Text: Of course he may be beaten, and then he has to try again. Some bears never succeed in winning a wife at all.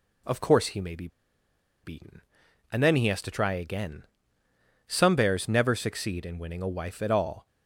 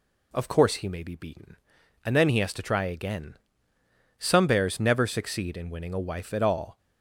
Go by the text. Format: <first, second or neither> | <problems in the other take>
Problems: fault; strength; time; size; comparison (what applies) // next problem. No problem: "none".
second | pauses between "be" and "beaten"; noticeable; at 1.0 s; 0.75 s long